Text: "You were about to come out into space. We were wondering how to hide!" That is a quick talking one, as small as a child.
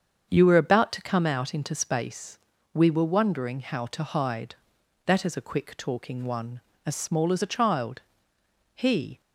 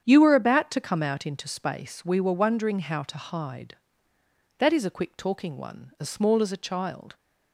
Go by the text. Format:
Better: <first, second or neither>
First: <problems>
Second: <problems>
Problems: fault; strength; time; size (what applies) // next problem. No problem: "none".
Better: second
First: starts louder than the rest; strong; until 1.3 s; 7.5 dB // goes on to say "He"; slight; from 8.7 s on; 0.46 s long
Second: starts louder than the rest; strong; until 1.0 s; 8.5 dB